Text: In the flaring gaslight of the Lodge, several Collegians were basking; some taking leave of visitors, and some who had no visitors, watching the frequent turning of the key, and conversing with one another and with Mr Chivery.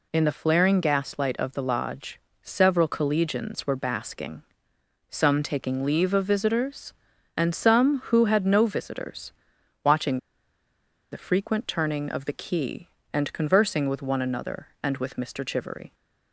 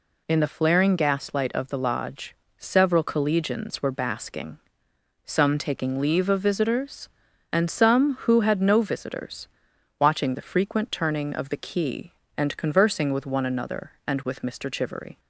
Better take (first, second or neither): second